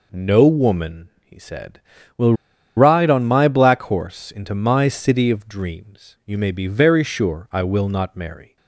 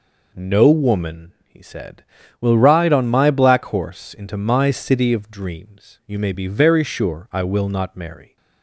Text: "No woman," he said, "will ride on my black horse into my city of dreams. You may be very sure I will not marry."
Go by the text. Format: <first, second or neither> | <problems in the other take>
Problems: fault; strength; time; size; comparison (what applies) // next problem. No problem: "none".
second | pauses between "will" and "ride"; at 2.3 s; 0.43 s long